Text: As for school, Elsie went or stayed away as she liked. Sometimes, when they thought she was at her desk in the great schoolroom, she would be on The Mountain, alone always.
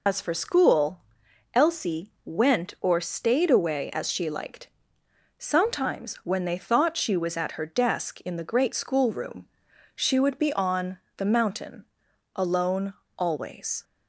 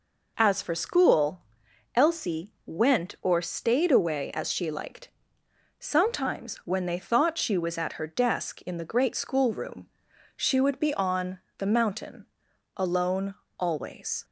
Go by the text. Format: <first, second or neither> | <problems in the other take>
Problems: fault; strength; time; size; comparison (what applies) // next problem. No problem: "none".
second | loses the start of "As"; at 0.0 s; 105 ms // pauses between "on" and "The"; slight; at 10.9 s; 0.20 s long; slight in the second // pauses between "alone" and "always"; slight; at 12.9 s; 0.24 s long; slight in the second